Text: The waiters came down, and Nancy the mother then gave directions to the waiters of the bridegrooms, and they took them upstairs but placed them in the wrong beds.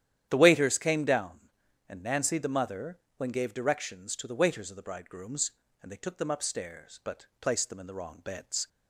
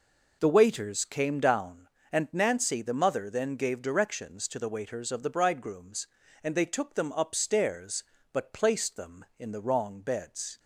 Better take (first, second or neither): second